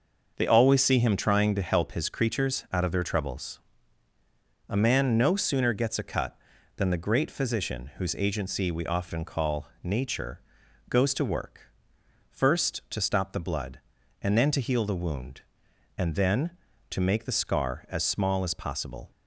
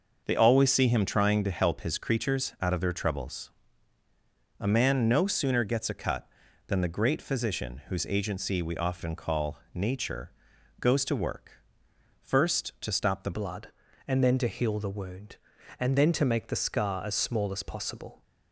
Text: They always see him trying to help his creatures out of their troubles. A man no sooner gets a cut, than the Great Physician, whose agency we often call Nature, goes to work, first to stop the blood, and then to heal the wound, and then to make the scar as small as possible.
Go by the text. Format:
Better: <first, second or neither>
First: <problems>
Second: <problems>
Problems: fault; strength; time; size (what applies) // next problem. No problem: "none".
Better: first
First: starts louder than the rest; noticeable; until 1.3 s; 6 dB // pauses between "call" and "Nature"; slight; at 9.6 s; 0.16 s long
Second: starts louder than the rest; noticeable; until 1.2 s; 6 dB // pauses between "call" and "Nature"; slight; at 9.5 s; 0.16 s long // changes voice at "blood"; from 13.3 s on; 4.9 s long